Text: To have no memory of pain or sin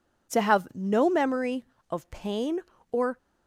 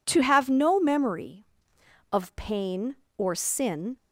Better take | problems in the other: second | stops before "sin"; at 3.1 s

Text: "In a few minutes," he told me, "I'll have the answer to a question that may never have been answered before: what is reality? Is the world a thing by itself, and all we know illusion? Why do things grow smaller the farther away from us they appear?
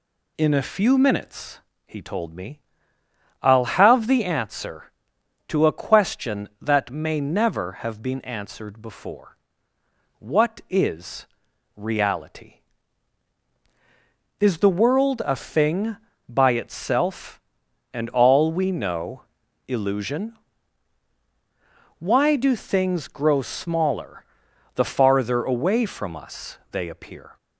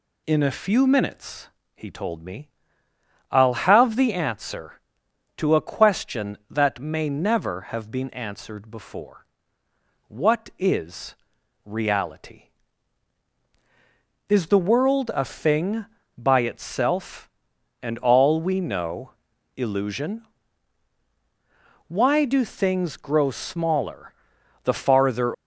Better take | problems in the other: first | pauses between "is" and "reality"; noticeable; at 11.1 s; 0.52 s long; noticeable in the first // pauses between "know" and "illusion"; noticeable; at 19.1 s; 0.46 s long; noticeable in the first // pauses between "smaller" and "the"; noticeable; at 24.1 s; 0.48 s long; noticeable in the first // stops before "away from us they appear"; at 25.3 s

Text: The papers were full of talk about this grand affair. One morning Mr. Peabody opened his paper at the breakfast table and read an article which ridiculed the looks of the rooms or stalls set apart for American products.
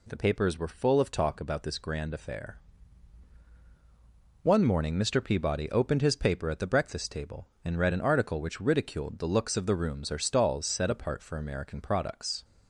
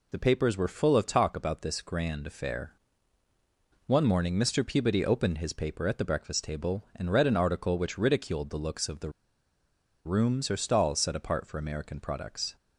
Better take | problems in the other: first | pauses between "the" and "rooms"; noticeable; at 9.1 s; 0.94 s long

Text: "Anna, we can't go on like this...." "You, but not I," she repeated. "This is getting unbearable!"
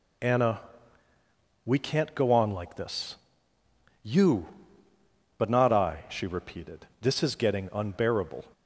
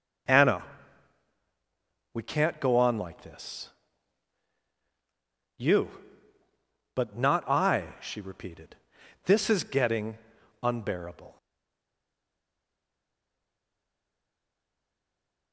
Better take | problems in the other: first | starts louder than the rest; until 2.7 s; 6.5 dB // pauses between "getting" and "unbearable"; at 10.1 s; 0.44 s long // stays silent after the last word; strong; from 11.3 s on; 4.2 s long

